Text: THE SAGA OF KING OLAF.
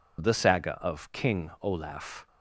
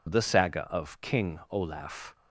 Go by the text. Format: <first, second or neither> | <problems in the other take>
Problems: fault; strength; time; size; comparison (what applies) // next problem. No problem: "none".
neither | none